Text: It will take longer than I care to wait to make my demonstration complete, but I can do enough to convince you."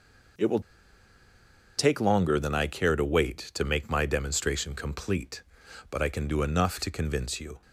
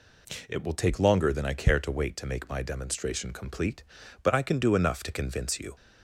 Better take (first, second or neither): second